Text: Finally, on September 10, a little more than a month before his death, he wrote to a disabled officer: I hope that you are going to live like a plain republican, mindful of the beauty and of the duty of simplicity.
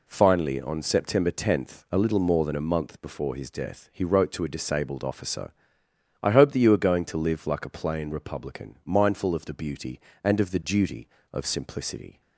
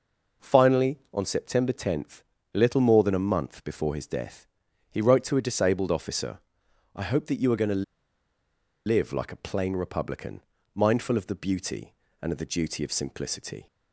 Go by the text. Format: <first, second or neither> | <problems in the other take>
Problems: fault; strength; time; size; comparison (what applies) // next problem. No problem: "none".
first | pauses between "to" and "live"; at 7.8 s; 1.0 s long